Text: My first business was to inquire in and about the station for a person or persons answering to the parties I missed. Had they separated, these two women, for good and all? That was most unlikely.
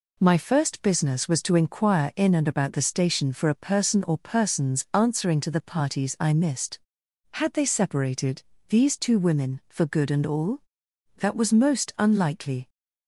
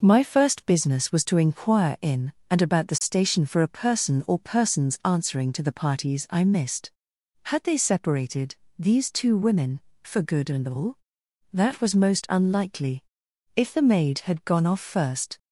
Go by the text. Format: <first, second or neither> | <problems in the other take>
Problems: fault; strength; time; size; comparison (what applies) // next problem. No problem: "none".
first | goes on to say "If the maid had gone off first"; strong; from 13.5 s on; 1.8 s long